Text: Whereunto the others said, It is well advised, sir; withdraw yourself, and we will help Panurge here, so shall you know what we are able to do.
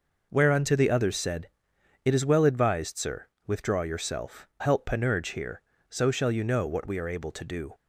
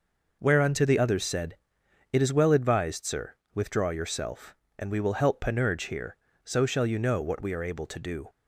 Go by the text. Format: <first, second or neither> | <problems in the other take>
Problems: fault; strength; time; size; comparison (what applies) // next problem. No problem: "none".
second | skips "and we will"; at 4.5 s